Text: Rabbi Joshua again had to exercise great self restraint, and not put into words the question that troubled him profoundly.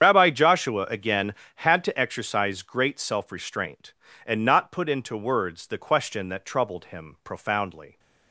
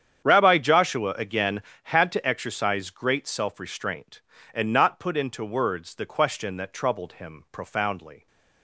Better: second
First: loses the start of "Rabbi"; at 0.0 s; 45 ms // starts louder than the rest; strong; until 1.1 s; 8.5 dB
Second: starts louder than the rest; strong; until 1.3 s; 8.5 dB

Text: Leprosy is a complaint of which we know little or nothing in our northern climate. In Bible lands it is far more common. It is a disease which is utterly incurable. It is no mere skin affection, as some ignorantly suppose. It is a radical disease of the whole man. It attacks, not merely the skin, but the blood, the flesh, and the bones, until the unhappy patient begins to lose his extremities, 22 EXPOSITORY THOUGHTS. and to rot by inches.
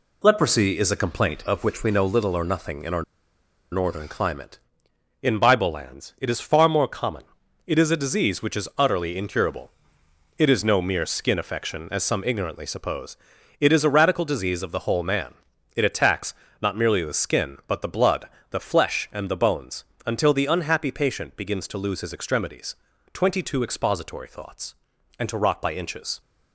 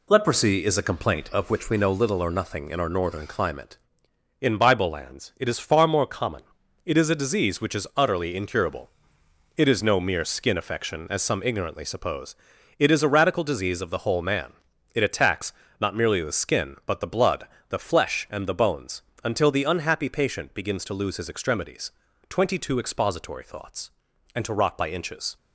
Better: second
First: pauses between "our" and "northern"; noticeable; at 3.0 s; 0.69 s long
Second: none

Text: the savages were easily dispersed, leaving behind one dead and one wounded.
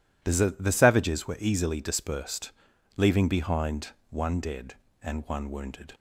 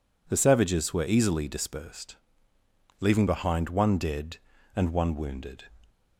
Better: second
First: says "the" twice; at 0.5 s // pauses between "behind" and "one"; slight; at 3.8 s; 0.22 s long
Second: none

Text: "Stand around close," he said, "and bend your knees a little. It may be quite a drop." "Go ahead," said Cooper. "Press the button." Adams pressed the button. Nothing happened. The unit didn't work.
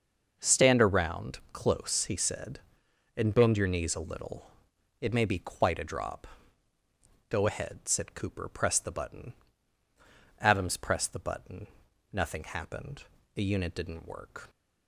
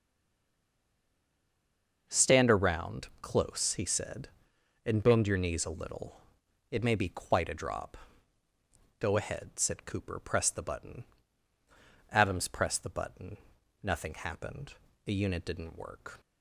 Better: first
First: starts louder than the rest; until 1.4 s; 6 dB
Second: stays silent before the first word; noticeable; until 2.0 s; 2.0 s long // starts louder than the rest; until 3.0 s; 6 dB

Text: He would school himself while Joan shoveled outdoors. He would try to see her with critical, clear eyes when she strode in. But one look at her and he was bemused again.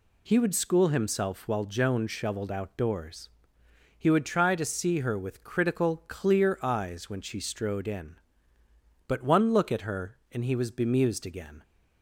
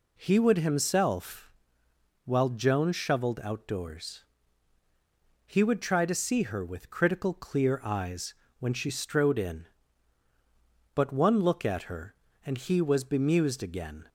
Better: first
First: none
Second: skips "school"; at 0.5 s // pauses between "himself" and "while"; noticeable; at 1.5 s; 0.72 s long // pauses between "eyes" and "when"; slight; at 8.3 s; 0.24 s long

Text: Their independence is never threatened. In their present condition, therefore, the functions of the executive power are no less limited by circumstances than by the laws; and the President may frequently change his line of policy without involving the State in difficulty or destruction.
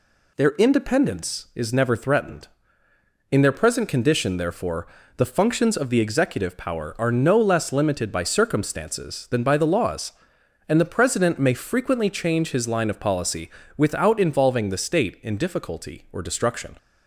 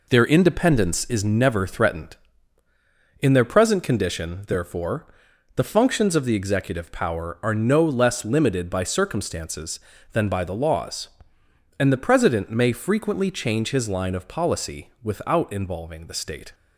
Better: first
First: pauses between "policy" and "without"; slight; at 13.4 s; 0.30 s long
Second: pauses between "policy" and "without"; slight; at 14.9 s; 0.20 s long // stops before "in difficulty or destruction"; at 16.5 s

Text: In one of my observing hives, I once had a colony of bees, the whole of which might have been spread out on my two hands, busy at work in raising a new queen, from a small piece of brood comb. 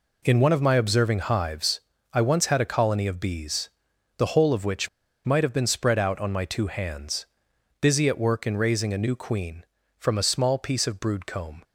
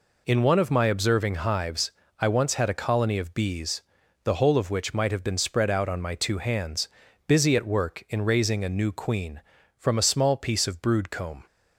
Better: second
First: pauses between "which" and "might"; at 4.8 s; 0.36 s long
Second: none

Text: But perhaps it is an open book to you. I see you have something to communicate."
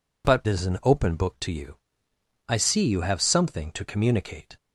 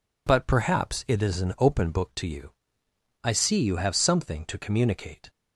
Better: second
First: skips "perhaps it"; at 0.4 s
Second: none

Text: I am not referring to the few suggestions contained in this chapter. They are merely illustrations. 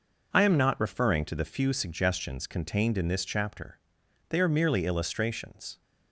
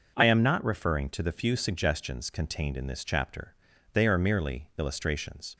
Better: neither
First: none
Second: none

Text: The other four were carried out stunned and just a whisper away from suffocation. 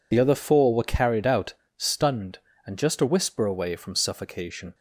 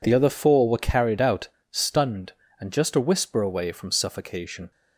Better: second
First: loses the start of "The"; at 0.1 s; 35 ms // pauses between "out" and "stunned"; slight; at 1.5 s; 0.24 s long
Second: pauses between "out" and "stunned"; slight; at 1.4 s; 0.23 s long

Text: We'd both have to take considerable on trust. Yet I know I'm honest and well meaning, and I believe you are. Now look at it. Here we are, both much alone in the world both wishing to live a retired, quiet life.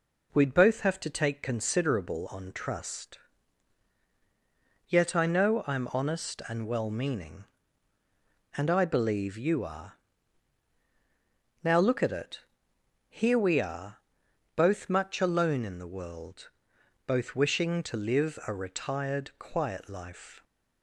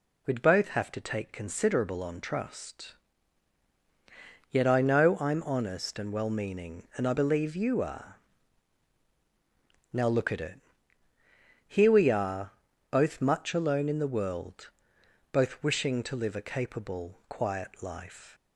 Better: first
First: pauses between "world" and "both"; noticeable; at 16.4 s; 0.58 s long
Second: pauses between "world" and "both"; noticeable; at 14.6 s; 0.62 s long // says "capable" for "retired"; at 16.4 s

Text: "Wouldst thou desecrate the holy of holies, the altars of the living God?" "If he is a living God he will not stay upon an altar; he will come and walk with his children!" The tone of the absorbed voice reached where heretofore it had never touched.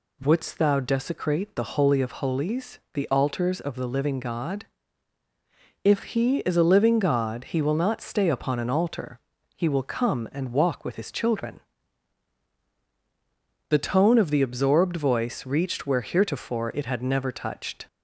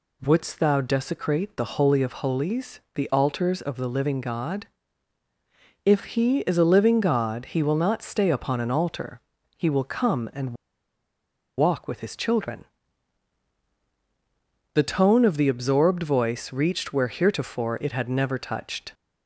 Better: first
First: none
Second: pauses between "and" and "walk"; at 10.5 s; 1.0 s long

